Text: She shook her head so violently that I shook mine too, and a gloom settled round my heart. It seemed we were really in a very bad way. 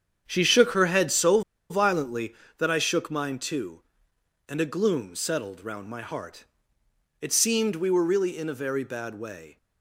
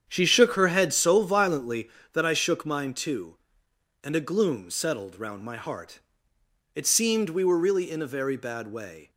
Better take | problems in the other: second | starts louder than the rest; strong; until 1.2 s; 8 dB; strong in the second // pauses between "so" and "violently"; slight; at 1.4 s; 0.29 s long

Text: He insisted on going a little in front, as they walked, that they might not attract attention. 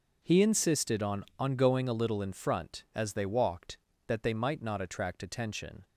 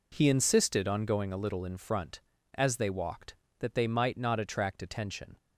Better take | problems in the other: second | says "on" twice; at 1.3 s

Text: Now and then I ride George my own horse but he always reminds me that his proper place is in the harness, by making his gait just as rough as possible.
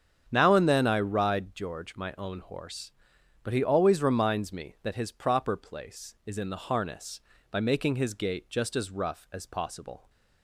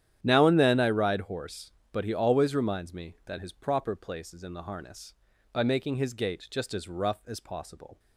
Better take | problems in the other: first | starts louder than the rest; strong; until 1.2 s; 10.5 dB; strong in the first // skips "George my own"; at 1.2 s

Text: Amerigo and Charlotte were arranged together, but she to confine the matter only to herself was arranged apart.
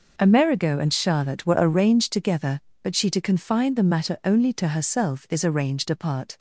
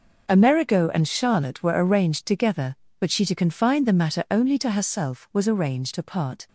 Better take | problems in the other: second | says "is" for "was"; at 5.2 s

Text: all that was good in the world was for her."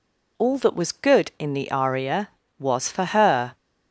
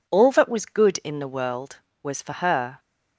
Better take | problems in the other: second | says "aria" for "world"; at 1.7 s

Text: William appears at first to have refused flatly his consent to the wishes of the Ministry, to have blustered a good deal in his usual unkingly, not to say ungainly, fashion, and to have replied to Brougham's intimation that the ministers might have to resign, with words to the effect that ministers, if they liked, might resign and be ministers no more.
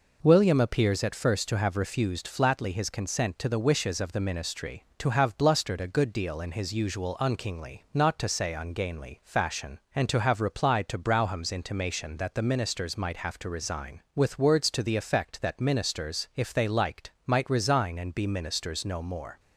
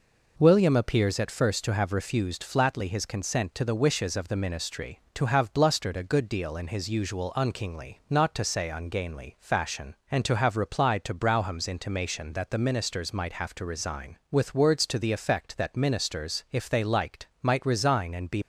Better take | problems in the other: first | stops before "ministers no more"; at 18.4 s

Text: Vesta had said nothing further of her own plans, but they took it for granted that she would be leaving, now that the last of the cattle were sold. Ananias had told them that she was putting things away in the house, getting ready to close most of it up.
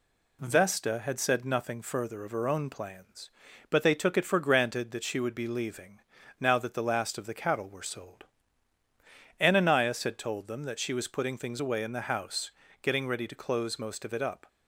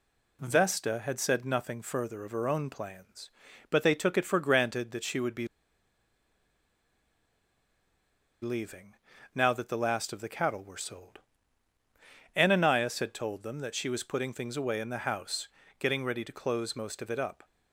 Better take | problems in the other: first | pauses between "be" and "leaving"; strong; at 5.4 s; 2.9 s long

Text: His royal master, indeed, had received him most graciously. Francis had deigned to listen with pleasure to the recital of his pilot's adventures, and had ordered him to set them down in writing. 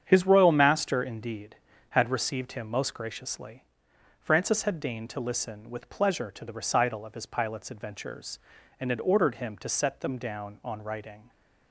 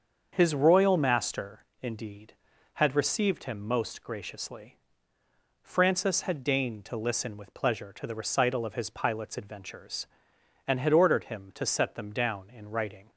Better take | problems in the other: second | starts louder than the rest; strong; until 1.0 s; 8 dB; also in the second // says "on" for "in"; at 10.6 s

